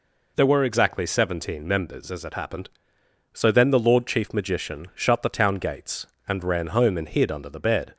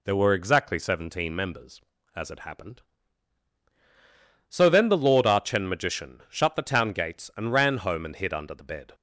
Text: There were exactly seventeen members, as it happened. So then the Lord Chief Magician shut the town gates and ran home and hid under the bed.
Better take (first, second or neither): first